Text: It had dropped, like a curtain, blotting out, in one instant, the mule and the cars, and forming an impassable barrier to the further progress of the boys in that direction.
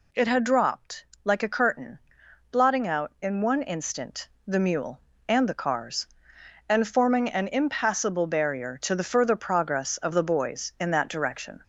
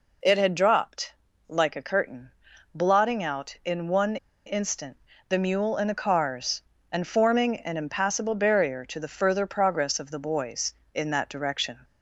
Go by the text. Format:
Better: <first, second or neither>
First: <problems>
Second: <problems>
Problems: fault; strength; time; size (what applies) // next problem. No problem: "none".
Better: first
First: none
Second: pauses between "one" and "instant"; slight; at 4.1 s; 0.29 s long